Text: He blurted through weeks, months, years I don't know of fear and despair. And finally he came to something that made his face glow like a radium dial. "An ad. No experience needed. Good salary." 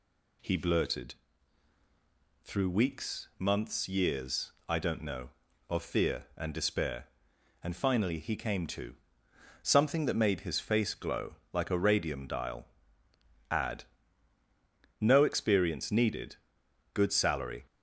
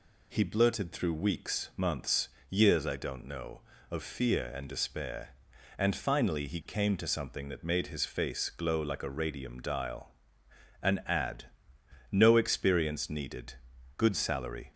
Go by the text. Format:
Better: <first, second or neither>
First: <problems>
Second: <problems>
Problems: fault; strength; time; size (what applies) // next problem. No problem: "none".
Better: second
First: pauses between "blurted" and "through"; strong; at 1.1 s; 1.2 s long // pauses between "years" and "I"; slight; at 4.5 s; 0.18 s long // pauses between "to" and "something"; noticeable; at 8.9 s; 0.66 s long // pauses between "glow" and "like"; slight; at 11.3 s; 0.16 s long // skips "An"; at 13.0 s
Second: none